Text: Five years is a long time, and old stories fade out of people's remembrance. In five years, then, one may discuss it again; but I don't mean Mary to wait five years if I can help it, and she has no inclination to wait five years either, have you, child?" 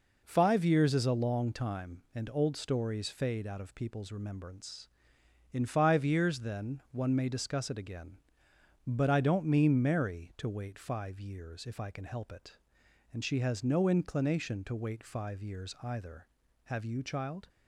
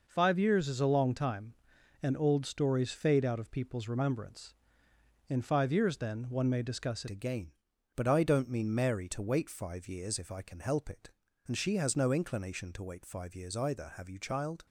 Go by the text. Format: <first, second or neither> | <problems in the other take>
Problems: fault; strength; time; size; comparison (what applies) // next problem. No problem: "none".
first | changes voice at "again"; from 7.0 s on; 7.6 s long